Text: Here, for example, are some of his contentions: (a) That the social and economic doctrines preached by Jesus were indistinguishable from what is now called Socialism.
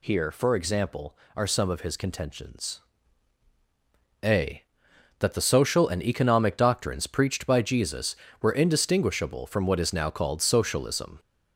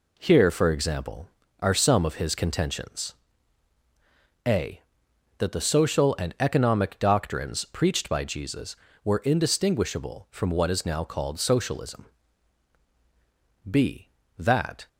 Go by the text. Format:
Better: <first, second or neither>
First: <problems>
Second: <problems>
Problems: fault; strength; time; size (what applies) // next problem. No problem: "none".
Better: first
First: none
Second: goes on to say "b That"; noticeable; from 13.6 s on; 1.1 s long